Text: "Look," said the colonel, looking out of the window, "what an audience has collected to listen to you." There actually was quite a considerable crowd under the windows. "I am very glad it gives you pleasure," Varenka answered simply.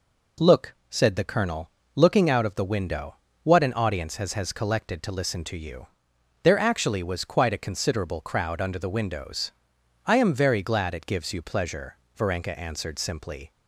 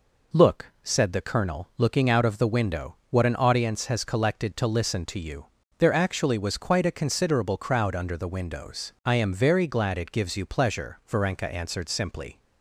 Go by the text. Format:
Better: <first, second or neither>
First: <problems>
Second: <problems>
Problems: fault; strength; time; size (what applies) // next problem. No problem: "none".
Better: second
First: says "has" twice; at 4.3 s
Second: none